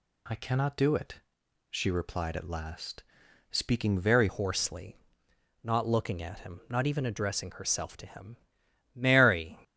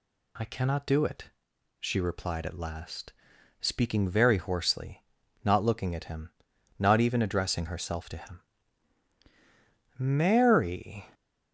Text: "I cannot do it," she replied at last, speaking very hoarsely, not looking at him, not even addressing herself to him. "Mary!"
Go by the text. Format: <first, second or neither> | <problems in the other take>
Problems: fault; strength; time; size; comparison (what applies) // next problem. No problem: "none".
second | changes voice at "hoarsely"; from 4.2 s on; 5.3 s long